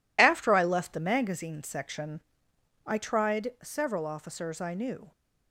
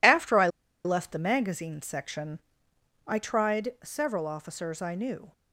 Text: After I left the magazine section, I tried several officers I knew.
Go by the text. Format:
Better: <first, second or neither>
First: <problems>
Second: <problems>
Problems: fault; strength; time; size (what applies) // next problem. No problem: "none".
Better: first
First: none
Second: pauses between "I" and "left"; at 0.4 s; 0.36 s long